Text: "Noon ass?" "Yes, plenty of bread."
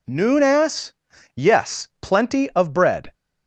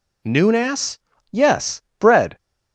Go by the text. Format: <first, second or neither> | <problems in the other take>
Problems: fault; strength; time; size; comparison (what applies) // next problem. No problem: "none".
first | skips "plenty of"; at 1.8 s